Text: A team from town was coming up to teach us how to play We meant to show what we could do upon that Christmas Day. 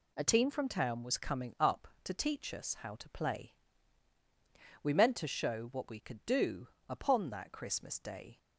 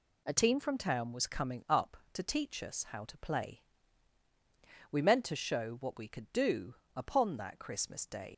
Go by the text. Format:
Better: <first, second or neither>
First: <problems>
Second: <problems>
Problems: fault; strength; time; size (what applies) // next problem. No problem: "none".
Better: first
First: pauses between "play" and "We"; strong; at 3.5 s; 1.2 s long // pauses between "do" and "upon"; slight; at 6.6 s; 0.20 s long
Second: pauses between "play" and "We"; strong; at 3.6 s; 1.2 s long // pauses between "do" and "upon"; slight; at 6.7 s; 0.20 s long // leaves "Day" unfinished; at 8.3 s; 100 ms